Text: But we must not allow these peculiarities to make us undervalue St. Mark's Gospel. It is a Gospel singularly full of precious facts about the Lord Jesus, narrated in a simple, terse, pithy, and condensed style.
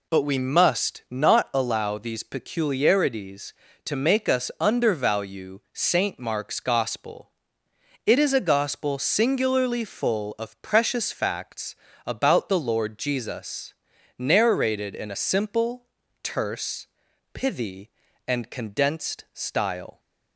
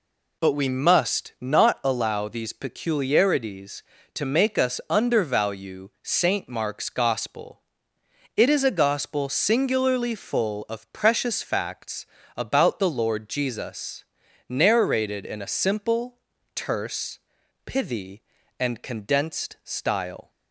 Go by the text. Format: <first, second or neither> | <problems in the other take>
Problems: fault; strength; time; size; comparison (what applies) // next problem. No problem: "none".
neither | pauses between "facts" and "about"; slight; the same in both